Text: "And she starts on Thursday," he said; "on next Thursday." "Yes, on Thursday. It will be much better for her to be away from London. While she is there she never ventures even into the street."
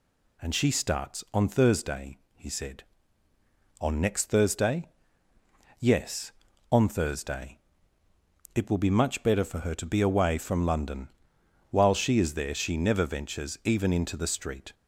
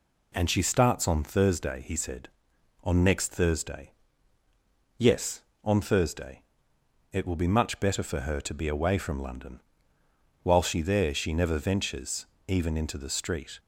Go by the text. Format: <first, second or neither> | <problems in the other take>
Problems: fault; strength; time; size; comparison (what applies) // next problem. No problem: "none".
first | skips "is"; at 10.8 s // pauses between "ventures" and "even"; slight; at 12.2 s; 0.22 s long